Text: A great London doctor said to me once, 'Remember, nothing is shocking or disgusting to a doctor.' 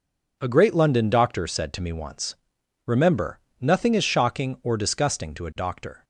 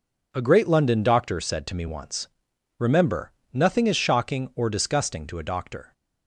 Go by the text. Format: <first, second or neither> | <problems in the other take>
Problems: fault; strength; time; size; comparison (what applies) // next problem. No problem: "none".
neither | none